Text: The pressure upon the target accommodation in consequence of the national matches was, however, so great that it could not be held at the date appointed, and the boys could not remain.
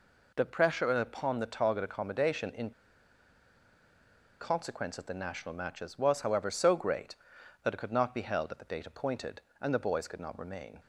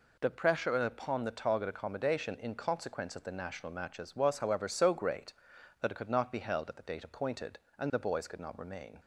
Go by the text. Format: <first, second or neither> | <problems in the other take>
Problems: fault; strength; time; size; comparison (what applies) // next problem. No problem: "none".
second | pauses between "in" and "consequence"; strong; at 2.7 s; 1.7 s long